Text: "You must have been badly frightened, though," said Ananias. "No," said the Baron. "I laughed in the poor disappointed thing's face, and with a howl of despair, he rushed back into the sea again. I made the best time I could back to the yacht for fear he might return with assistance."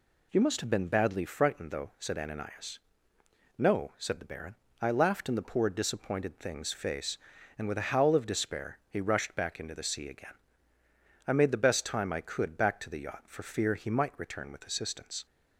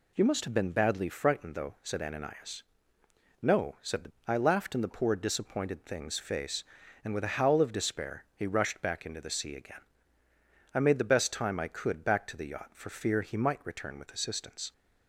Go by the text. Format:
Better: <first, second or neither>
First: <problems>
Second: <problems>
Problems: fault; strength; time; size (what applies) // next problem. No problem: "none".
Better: first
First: none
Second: skips "Baron"; at 4.1 s